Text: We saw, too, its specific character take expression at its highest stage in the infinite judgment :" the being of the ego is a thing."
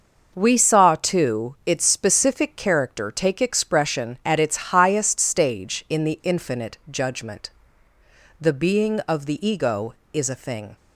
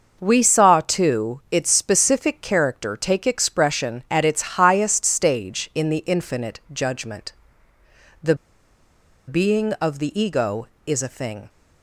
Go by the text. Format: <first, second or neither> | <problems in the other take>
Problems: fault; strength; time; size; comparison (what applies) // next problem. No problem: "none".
first | starts louder than the rest; noticeable; until 1.2 s; 6 dB; noticeable in the first // pauses between "the" and "being"; noticeable; at 8.3 s; 0.93 s long